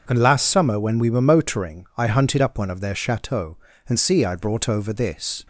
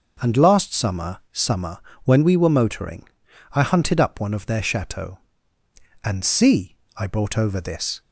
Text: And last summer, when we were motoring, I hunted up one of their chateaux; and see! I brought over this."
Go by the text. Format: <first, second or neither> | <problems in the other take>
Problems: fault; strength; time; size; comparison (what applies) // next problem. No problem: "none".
first | says "summer" twice; at 1.3 s